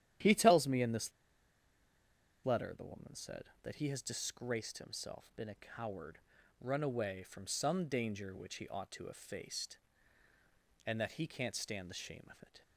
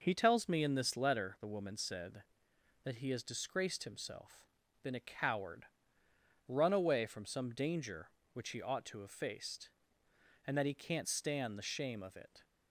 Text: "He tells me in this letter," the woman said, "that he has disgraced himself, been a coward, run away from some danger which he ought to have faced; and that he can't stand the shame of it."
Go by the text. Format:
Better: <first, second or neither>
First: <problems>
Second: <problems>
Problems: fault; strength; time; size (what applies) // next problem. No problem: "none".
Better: second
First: starts louder than the rest; strong; until 2.5 s; 11.5 dB // pauses between "this" and "letter"; strong; at 1.1 s; 1.3 s long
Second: none